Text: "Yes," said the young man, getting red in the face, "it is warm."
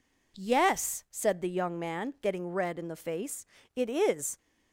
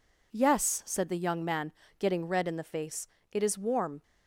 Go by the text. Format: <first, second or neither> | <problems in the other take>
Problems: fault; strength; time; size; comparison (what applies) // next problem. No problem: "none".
second | stops before "warm"; at 4.3 s